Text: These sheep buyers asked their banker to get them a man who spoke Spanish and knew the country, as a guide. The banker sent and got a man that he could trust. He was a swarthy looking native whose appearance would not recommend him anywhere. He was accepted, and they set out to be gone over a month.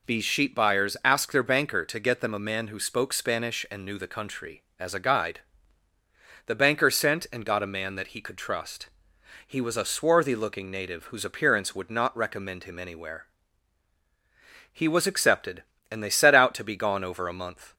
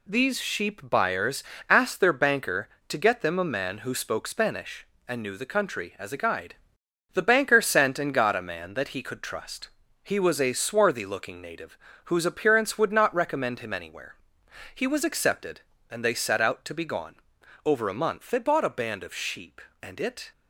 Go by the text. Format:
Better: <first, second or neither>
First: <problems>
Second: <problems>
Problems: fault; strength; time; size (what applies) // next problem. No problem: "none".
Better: first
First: none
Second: pauses between "buyers" and "asked"; slight; at 1.4 s; 0.26 s long // pauses between "native" and "whose"; slight; at 11.7 s; 0.28 s long // pauses between "gone" and "over"; noticeable; at 17.1 s; 0.50 s long // goes on to say "They bought a band of sheep and it"; strong; from 18.2 s on; 2.0 s long